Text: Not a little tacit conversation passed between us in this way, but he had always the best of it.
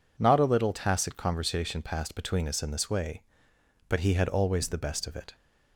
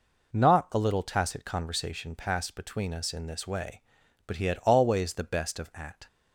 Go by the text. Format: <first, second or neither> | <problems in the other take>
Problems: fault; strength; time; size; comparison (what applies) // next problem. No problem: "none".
first | says "at" for "it"; at 5.7 s